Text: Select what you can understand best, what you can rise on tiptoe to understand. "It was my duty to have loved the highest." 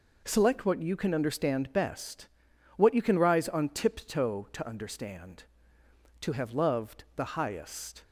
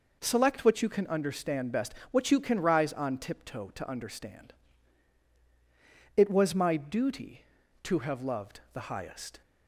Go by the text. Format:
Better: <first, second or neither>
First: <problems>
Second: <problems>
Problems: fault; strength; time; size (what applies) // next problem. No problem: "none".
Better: second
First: skips "It was my duty"; at 5.8 s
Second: none